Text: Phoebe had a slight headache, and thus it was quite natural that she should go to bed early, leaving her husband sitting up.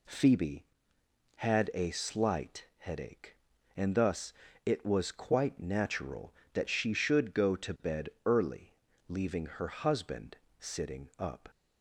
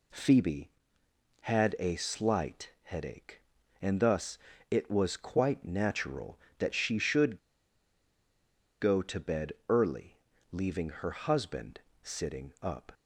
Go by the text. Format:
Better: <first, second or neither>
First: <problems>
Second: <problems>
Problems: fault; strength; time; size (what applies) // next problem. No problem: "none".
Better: first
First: pauses between "thus" and "it"; slight; at 4.3 s; 0.32 s long // pauses between "bed" and "early"; slight; at 8.0 s; 0.16 s long // pauses between "husband" and "sitting"; slight; at 10.3 s; 0.22 s long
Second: pauses between "thus" and "it"; slight; at 4.3 s; 0.32 s long // pauses between "should" and "go"; strong; at 7.3 s; 1.4 s long // pauses between "bed" and "early"; slight; at 9.5 s; 0.16 s long // pauses between "husband" and "sitting"; slight; at 11.8 s; 0.22 s long